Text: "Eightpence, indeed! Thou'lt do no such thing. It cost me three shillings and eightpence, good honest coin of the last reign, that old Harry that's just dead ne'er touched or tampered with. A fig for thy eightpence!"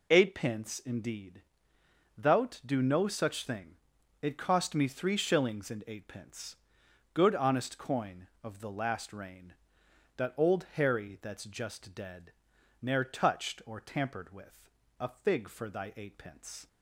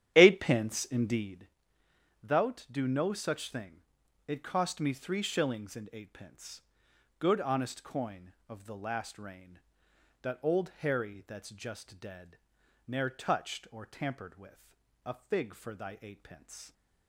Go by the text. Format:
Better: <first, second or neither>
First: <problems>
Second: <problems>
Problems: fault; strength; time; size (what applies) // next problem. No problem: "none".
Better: first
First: pauses between "dead" and "ne'er"; noticeable; at 12.3 s; 0.52 s long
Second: starts louder than the rest; strong; until 1.5 s; 10.5 dB // pauses between "dead" and "ne'er"; noticeable; at 12.3 s; 0.52 s long